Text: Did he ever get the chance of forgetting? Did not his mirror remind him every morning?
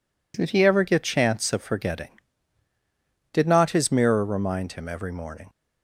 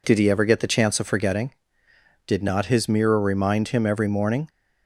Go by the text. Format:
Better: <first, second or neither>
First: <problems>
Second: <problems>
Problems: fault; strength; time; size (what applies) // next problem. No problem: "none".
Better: second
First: skips "the"; at 1.0 s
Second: none